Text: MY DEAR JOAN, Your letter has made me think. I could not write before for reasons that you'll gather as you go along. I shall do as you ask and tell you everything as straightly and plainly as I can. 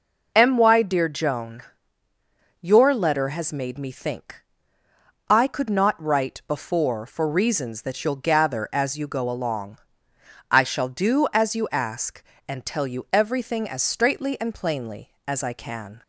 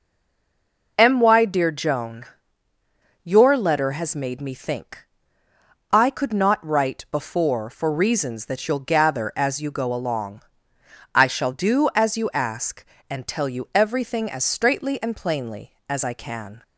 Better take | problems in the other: first | stays silent before the first word; slight; until 0.9 s; 0.9 s long

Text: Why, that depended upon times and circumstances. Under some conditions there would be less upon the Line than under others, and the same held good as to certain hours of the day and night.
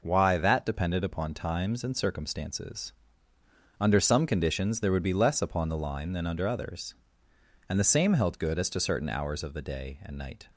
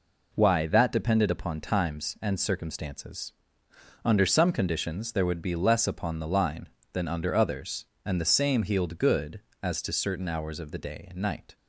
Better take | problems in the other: first | says "healed" for "held"; at 8.6 s

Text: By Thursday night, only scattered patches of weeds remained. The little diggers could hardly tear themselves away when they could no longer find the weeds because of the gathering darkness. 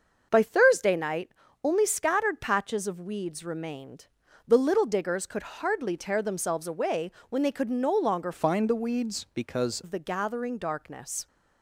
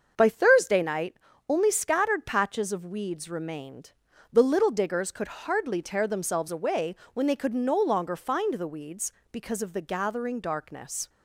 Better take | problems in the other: second | starts louder than the rest; until 1.3 s; 6.5 dB; also in the second // pauses between "away" and "when"; slight; at 7.1 s; 0.20 s long; slight in the second // changes voice from "find" to "because"; from 8.3 to 9.8 s; 1.5 s long

